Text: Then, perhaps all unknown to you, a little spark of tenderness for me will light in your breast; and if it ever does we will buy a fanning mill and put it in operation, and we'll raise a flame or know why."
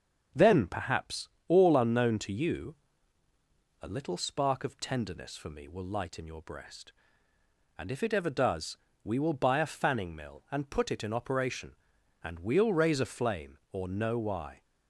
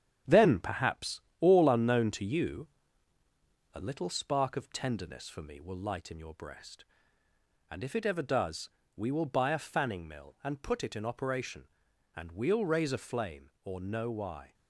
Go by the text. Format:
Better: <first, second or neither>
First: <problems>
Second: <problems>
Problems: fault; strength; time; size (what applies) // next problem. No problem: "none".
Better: first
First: starts louder than the rest; until 1.5 s; 6.5 dB // pauses between "perhaps" and "all"; slight; at 1.2 s; 0.20 s long // pauses between "does" and "we"; slight; at 8.7 s; 0.26 s long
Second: gets quieter; noticeable; throughout; 6 dB // starts louder than the rest; strong; until 1.4 s; 9 dB // pauses between "perhaps" and "all"; slight; at 1.1 s; 0.20 s long // pauses between "does" and "we"; slight; at 8.6 s; 0.26 s long